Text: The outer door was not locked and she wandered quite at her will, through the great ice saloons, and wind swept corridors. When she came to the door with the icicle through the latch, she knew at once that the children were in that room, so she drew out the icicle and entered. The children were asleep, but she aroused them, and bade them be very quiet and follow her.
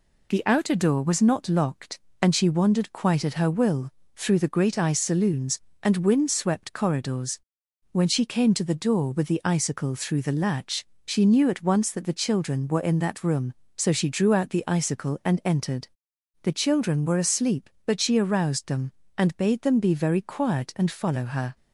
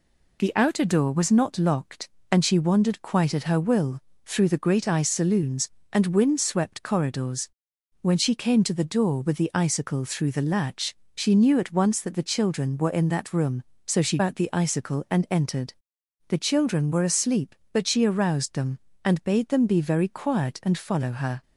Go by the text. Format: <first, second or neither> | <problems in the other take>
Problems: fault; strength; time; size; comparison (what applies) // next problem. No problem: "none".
first | skips "drew"; at 14.1 s